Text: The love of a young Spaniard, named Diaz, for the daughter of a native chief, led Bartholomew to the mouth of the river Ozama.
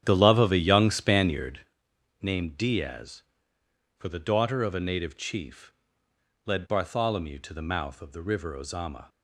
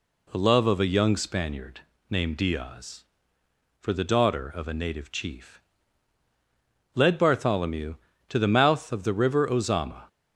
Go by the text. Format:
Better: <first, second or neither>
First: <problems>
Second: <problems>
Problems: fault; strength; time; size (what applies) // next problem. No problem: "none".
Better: second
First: starts louder than the rest; strong; until 1.8 s; 10 dB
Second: none